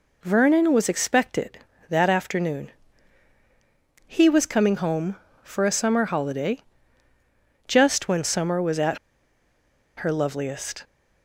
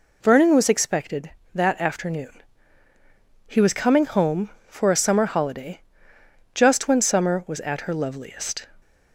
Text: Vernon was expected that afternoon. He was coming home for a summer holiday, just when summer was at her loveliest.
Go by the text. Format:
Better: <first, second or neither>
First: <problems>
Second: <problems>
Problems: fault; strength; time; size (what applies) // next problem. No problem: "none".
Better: second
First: pauses between "at" and "her"; at 8.9 s; 0.99 s long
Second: none